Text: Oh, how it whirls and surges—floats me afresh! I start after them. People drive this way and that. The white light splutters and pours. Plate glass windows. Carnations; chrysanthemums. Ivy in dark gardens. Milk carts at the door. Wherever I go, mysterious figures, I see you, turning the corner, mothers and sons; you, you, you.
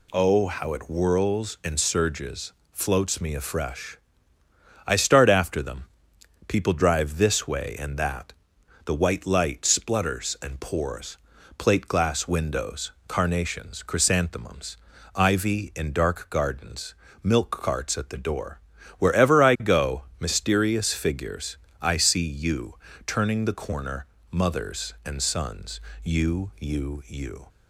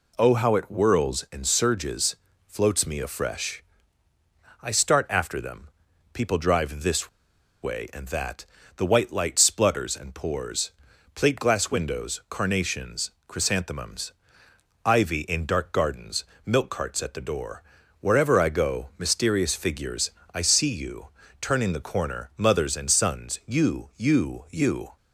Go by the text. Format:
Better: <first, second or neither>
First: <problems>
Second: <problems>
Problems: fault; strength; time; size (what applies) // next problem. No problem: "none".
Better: first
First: none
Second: pauses between "this" and "way"; noticeable; at 7.0 s; 0.53 s long